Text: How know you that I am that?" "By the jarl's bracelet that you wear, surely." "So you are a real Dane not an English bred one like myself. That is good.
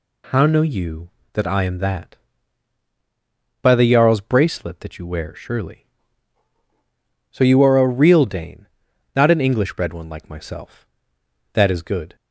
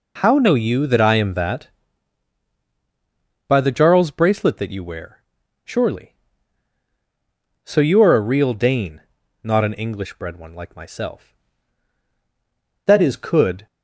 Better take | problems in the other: first | pauses between "Dane" and "not"; at 9.0 s; 0.40 s long; noticeable in the first // says "could" for "good"; at 13.1 s

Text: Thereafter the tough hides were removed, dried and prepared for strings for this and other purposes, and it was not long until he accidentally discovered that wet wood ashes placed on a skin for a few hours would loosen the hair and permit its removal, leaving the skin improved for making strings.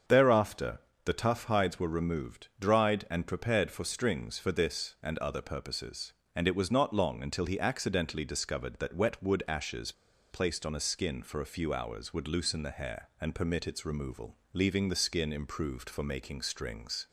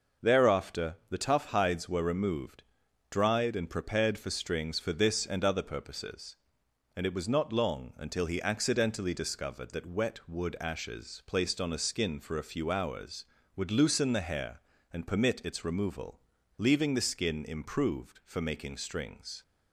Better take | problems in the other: second | starts louder than the rest; until 1.3 s; 7 dB // pauses between "Thereafter" and "the"; slight; at 0.8 s; 0.26 s long // pauses between "ashes" and "placed"; at 9.9 s; 0.38 s long

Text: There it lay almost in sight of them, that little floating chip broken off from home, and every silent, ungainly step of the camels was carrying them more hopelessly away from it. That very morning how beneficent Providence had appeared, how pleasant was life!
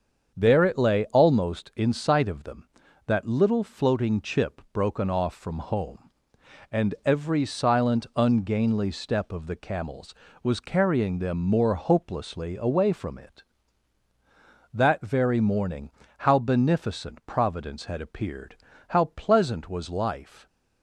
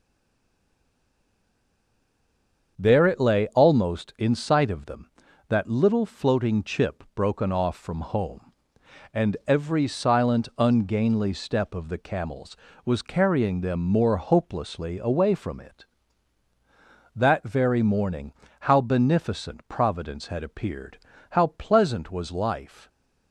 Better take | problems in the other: first | stays silent before the first word; strong; until 2.7 s; 2.7 s long // starts louder than the rest; until 3.7 s; 7 dB; also in the first // pauses between "morning" and "how"; slight; at 18.3 s; 0.28 s long; slight in the first

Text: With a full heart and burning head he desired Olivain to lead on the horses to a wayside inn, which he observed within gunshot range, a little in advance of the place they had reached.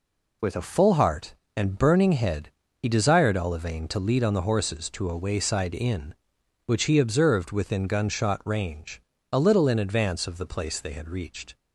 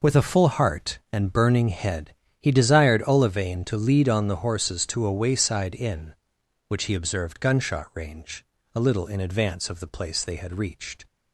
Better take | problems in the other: first | pauses between "head" and "he"; slight; at 2.1 s; 0.28 s long; slight in the first // skips "within"; at 7.3 s

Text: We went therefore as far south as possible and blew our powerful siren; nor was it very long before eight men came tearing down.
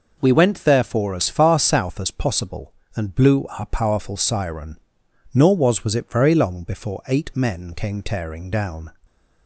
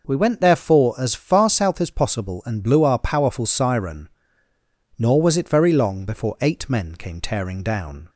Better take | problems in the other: second | says "was" twice; at 5.8 s

